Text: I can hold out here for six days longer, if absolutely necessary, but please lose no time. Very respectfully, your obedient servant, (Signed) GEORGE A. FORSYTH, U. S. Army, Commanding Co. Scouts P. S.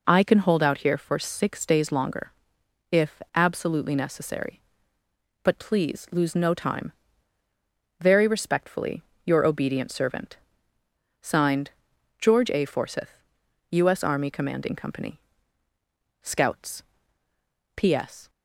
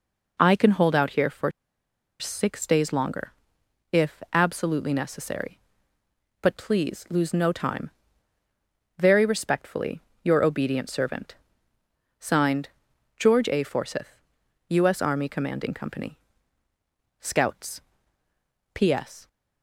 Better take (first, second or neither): first